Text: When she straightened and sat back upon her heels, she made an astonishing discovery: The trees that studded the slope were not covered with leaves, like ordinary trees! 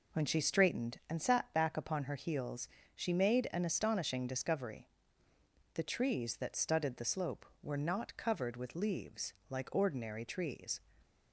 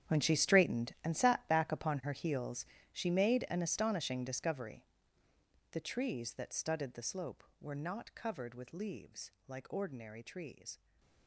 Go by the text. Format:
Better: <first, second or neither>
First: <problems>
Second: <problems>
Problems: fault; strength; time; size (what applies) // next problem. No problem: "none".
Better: first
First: none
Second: gets quieter; strong; throughout; 15.5 dB // stays silent after the last word; slight; from 10.7 s on; 0.5 s long